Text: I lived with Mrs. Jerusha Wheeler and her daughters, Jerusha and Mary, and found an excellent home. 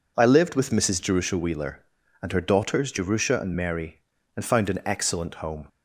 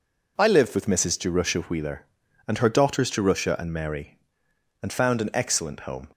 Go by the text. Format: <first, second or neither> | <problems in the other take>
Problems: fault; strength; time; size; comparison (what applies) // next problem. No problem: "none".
neither | none